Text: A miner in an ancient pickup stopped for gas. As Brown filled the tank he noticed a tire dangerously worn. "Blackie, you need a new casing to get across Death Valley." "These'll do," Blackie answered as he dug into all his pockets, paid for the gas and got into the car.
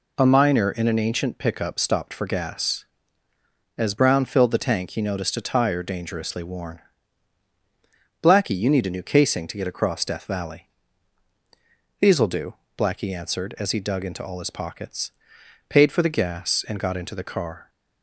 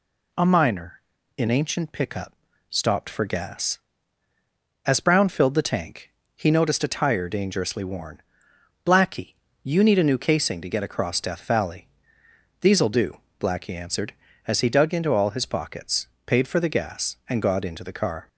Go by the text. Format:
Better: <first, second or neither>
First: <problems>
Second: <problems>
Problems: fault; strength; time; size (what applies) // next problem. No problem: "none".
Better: first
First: none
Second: skips "an"; at 1.4 s // pauses between "pickup" and "stopped"; slight; at 2.3 s; 0.36 s long // pauses between "tank" and "he"; slight; at 6.0 s; 0.26 s long